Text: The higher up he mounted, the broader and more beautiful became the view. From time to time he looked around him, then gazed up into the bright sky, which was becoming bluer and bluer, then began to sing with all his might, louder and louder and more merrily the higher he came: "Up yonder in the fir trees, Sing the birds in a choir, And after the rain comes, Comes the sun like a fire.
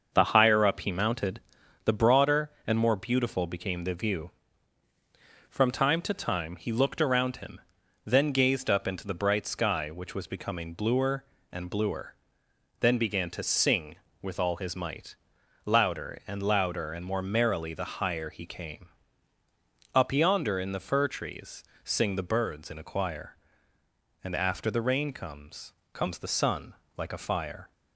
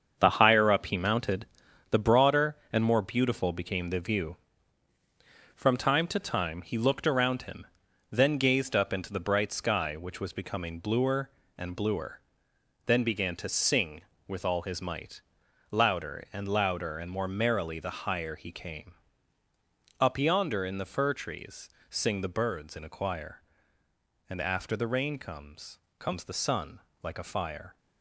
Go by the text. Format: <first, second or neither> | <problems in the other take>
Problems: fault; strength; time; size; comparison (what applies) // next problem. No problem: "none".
first | gets quieter; strong; throughout; 8.5 dB // starts louder than the rest; until 1.1 s; 7 dB; also in the first // pauses between "sun" and "like"; slight; at 26.8 s; 0.22 s long; slight in the first